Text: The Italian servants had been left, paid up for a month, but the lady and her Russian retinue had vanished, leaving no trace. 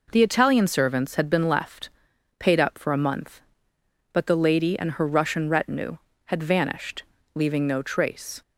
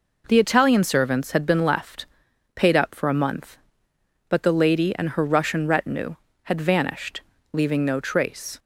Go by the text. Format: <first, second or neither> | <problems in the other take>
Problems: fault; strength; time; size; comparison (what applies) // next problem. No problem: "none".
neither | none